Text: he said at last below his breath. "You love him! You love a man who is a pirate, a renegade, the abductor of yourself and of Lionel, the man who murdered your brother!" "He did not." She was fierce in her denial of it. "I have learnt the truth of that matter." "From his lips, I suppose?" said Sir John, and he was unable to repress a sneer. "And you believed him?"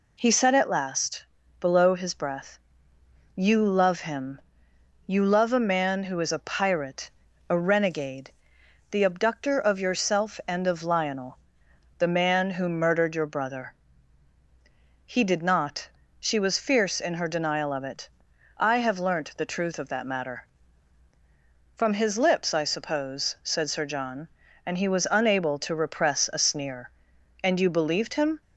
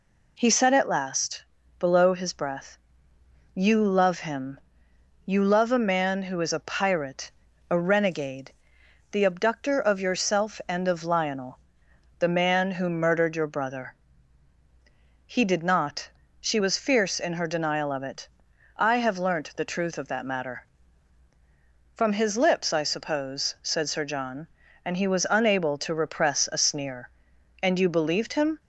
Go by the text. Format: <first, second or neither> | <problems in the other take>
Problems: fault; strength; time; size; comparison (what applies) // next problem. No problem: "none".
neither | pauses between "last" and "below"; slight; the same in both